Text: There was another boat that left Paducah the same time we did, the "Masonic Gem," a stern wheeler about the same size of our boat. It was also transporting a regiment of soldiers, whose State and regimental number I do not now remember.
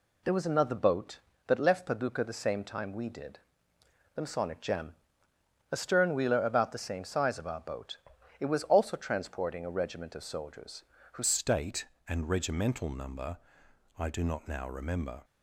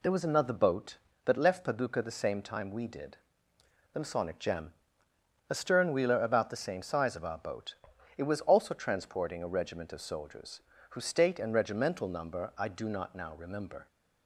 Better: second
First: changes voice at "State"; from 11.2 s on; 4.0 s long // pauses between "number" and "I"; noticeable; at 13.3 s; 0.60 s long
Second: none

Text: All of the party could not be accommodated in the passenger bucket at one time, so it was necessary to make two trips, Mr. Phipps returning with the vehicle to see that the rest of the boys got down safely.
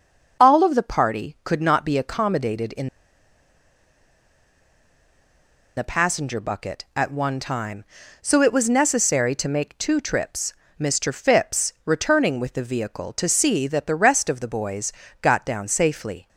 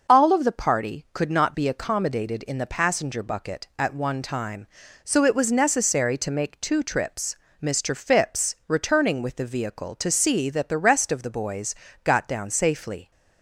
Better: second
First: pauses between "in" and "the"; strong; at 2.8 s; 2.8 s long // pauses between "boys" and "got"; slight; at 14.9 s; 0.30 s long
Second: pauses between "boys" and "got"; slight; at 11.7 s; 0.30 s long

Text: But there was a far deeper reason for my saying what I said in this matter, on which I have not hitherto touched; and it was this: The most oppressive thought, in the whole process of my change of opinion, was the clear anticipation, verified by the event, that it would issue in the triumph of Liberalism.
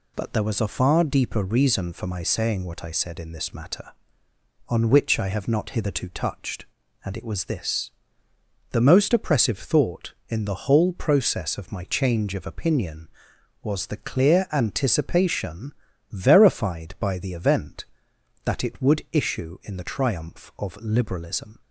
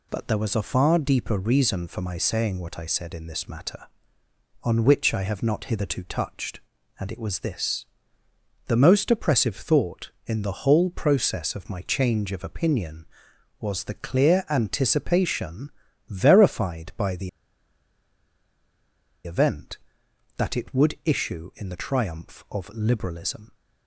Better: first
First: none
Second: pauses between "the" and "event"; strong; at 17.2 s; 1.9 s long

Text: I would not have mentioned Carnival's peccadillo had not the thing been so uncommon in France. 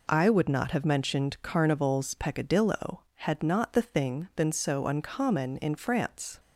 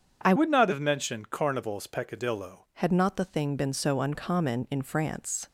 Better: first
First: none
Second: starts louder than the rest; strong; until 1.2 s; 7.5 dB // changes voice from "would" to "peccadillo"; from 0.3 to 2.6 s; 2.3 s long

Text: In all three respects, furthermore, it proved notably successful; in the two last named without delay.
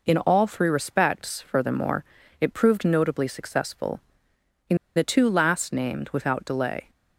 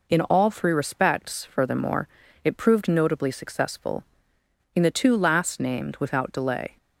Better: second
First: pauses between "in" and "the"; slight; at 4.7 s; 0.18 s long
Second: none

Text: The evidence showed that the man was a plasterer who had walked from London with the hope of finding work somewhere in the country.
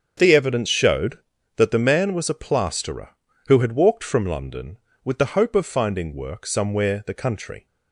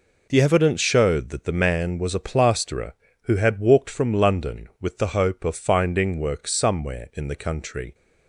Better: second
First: starts louder than the rest; strong; until 1.5 s; 7 dB // skips "in"; at 7.0 s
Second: none

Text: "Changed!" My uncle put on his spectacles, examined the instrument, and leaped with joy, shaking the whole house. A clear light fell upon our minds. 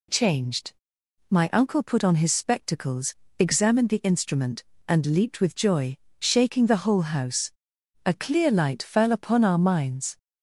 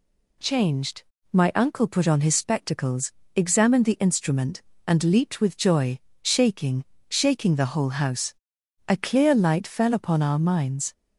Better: first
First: none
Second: says "shaking" twice; at 7.0 s

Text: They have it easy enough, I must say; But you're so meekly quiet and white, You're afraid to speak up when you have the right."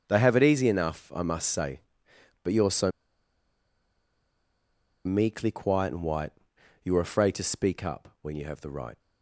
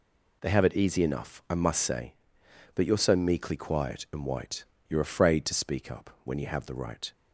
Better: second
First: starts louder than the rest; strong; until 1.0 s; 7 dB // pauses between "so" and "meekly"; strong; at 2.9 s; 2.1 s long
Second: none

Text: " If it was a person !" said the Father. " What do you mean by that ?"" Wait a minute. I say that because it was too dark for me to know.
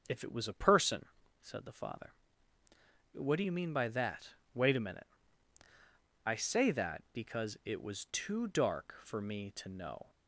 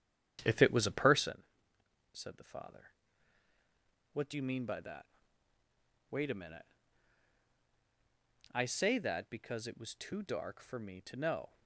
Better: first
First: none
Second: starts louder than the rest; strong; until 1.4 s; 10.5 dB

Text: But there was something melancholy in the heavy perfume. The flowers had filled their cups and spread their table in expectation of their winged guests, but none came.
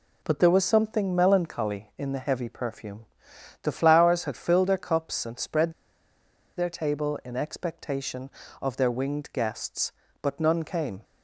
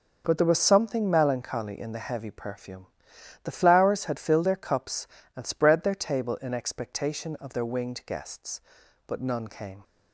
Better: second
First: pauses between "spread" and "their"; noticeable; at 5.7 s; 0.84 s long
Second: none

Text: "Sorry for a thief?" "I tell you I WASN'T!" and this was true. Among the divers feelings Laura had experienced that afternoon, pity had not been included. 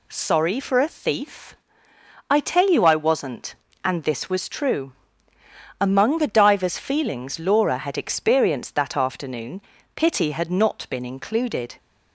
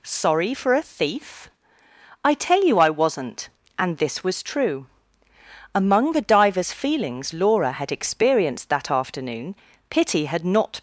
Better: first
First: none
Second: stops before "been included"; at 10.7 s

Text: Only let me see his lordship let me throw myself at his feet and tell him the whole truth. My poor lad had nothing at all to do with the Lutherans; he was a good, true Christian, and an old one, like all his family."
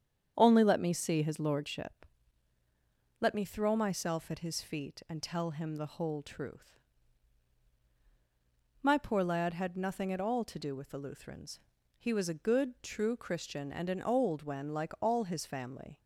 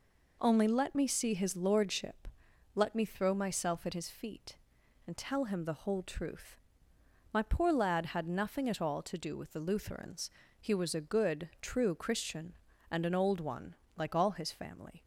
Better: second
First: starts louder than the rest; strong; until 1.3 s; 8 dB // pauses between "lordship" and "let"; at 2.0 s; 1.1 s long // says "when" for "one"; at 14.4 s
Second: pauses between "lordship" and "let"; noticeable; at 2.2 s; 0.46 s long

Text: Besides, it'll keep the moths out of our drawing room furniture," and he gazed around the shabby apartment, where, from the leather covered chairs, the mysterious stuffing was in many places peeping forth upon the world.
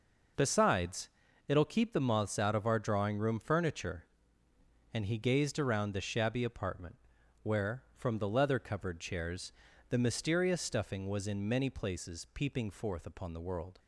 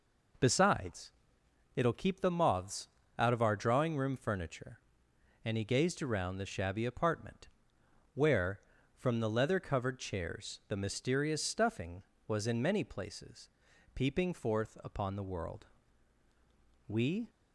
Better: first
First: none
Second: pauses between "moths" and "out"; slight; at 2.8 s; 0.30 s long // pauses between "places" and "peeping"; noticeable; at 13.4 s; 0.46 s long // goes on to say "We"; slight; from 16.8 s on; 0.44 s long

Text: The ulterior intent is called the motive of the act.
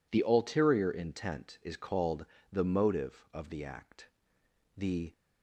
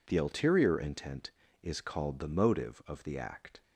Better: second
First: pauses between "called" and "the"; slight; at 2.2 s; 0.26 s long // goes on to say "The"; slight; from 4.7 s on; 0.38 s long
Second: none

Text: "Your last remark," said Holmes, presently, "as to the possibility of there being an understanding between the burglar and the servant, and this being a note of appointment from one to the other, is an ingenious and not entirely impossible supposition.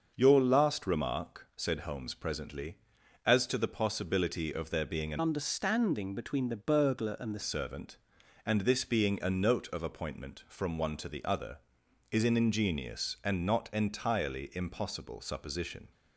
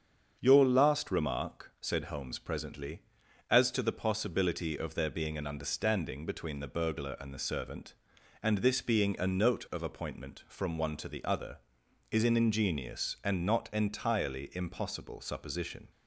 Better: second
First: starts louder than the rest; until 1.1 s; 6.5 dB // changes voice from "understanding" to "the"; from 5.1 to 7.4 s; 2.3 s long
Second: starts louder than the rest; until 1.4 s; 7 dB

